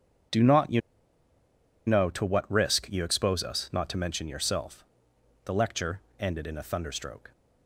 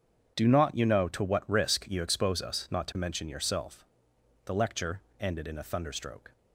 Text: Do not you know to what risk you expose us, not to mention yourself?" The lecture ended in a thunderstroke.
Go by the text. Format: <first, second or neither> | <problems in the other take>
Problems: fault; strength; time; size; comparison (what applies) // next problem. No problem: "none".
second | starts louder than the rest; strong; until 2.4 s; 8 dB; strong in the second // pauses between "you" and "know"; at 0.8 s; 1.0 s long // pauses between "lecture" and "ended"; slight; at 6.0 s; 0.18 s long; slight in the second